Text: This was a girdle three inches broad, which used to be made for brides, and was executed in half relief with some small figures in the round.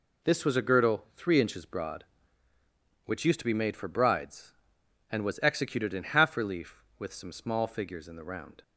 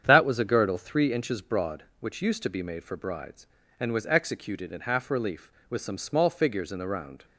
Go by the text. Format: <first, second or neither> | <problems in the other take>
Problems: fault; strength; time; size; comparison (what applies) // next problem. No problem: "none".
first | starts louder than the rest; strong; until 1.0 s; 8 dB // says "That" for "This"; at 0.0 s